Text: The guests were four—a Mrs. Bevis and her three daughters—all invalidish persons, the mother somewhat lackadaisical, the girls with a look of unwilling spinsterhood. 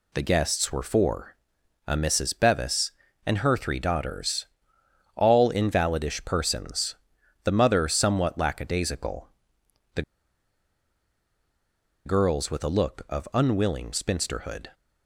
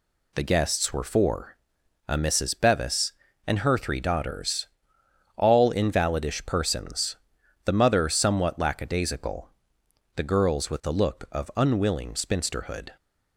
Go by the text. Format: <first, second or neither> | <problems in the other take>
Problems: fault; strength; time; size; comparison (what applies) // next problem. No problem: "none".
second | pauses between "the" and "girls"; strong; at 10.0 s; 2.0 s long